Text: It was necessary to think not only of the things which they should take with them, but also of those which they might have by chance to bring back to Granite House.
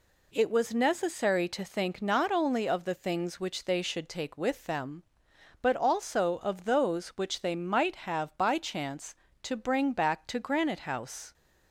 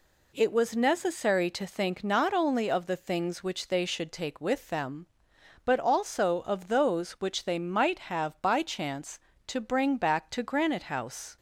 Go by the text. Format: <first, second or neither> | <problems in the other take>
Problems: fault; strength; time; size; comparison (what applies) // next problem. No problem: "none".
neither | none